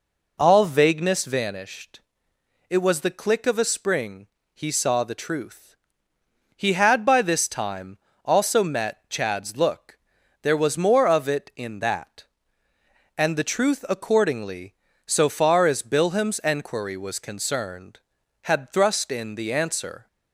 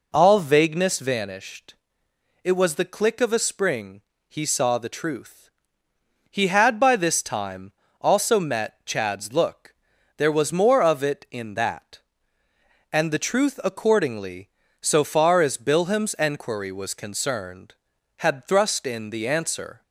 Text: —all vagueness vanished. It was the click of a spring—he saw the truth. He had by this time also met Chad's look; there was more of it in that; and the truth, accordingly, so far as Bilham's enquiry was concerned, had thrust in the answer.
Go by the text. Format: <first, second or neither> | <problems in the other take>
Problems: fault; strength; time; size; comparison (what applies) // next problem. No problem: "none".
neither | pauses between "time" and "also"; slight; the same in both